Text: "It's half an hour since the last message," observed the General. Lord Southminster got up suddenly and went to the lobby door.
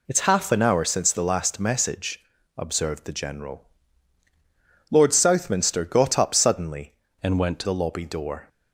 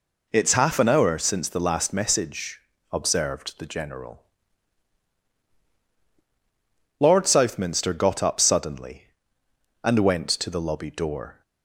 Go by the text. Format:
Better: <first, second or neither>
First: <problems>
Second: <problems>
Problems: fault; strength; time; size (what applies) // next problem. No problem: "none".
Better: second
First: changes voice from "and" to "to"; from 7.2 to 7.6 s; 0.4 s long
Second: none